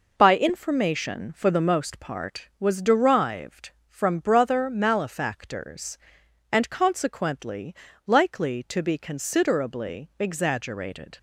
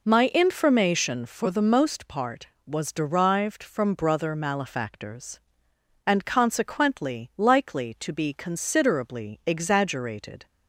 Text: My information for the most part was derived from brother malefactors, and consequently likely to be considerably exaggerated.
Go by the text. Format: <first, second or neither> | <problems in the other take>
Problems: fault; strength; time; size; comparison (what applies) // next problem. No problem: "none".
second | says "By" for "My"; at 0.1 s // pauses between "consequently" and "likely"; slight; at 7.7 s; 0.32 s long